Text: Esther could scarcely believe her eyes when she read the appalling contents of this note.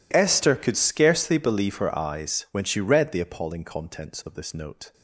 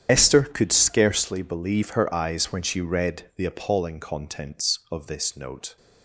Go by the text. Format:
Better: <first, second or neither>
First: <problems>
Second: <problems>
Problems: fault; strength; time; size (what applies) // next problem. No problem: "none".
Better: first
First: none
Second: loses the start of "Esther"; at 0.0 s; 45 ms // starts louder than the rest; strong; until 1.1 s; 9.5 dB